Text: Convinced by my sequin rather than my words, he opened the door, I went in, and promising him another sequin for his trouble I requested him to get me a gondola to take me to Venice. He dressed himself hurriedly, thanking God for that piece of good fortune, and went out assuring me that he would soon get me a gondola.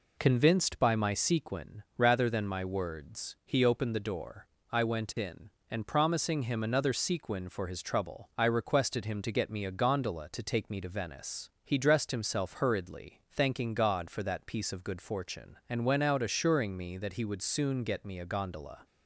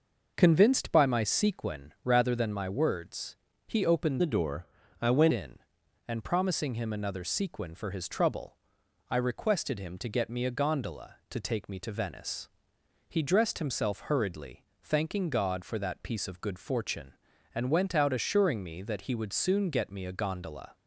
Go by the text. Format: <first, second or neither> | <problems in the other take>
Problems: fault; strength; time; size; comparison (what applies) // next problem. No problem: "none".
first | changes voice from "the" to "went"; from 4.2 to 5.3 s; 1.1 s long // pauses between "trouble" and "I"; noticeable; at 8.5 s; 0.52 s long